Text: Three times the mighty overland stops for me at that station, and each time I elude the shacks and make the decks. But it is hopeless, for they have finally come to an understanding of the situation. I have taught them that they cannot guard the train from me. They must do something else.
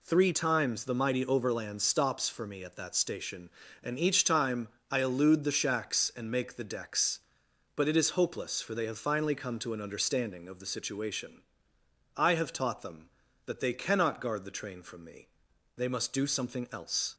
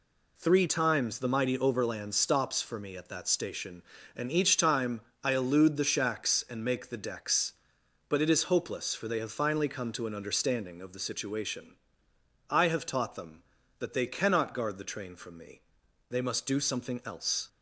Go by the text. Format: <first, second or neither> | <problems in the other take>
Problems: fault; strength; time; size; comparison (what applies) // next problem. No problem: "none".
neither | pauses between "time" and "I"; slight; the same in both